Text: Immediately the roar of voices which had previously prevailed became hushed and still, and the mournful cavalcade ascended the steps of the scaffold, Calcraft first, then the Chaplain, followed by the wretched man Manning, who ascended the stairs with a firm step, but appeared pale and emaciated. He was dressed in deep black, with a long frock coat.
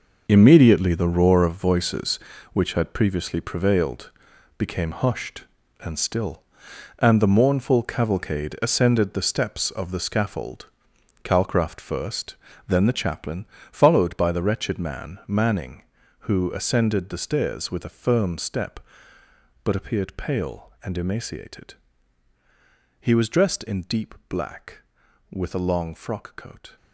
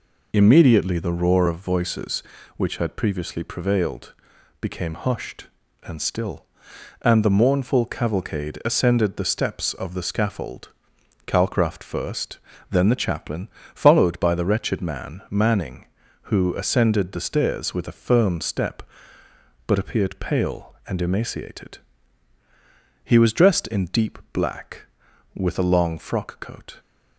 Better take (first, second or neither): second